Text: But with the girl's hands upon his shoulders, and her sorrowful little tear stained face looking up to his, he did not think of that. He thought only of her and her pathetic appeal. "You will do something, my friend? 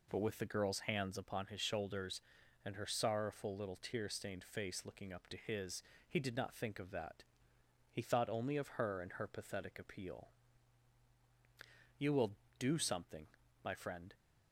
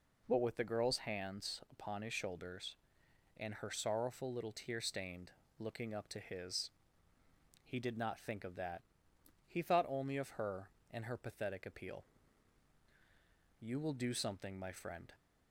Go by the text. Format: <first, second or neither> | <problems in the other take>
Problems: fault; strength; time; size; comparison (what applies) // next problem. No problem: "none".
first | skips "face"; at 5.4 s